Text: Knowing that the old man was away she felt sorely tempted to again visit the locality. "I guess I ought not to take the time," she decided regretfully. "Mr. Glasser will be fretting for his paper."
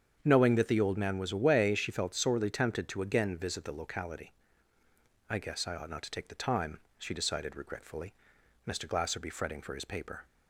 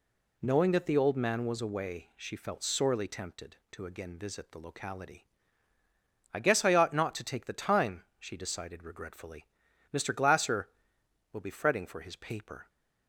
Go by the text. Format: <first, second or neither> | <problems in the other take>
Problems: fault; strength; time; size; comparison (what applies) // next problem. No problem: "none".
second | starts louder than the rest; strong; until 1.2 s; 7.5 dB // skips "will"; at 9.2 s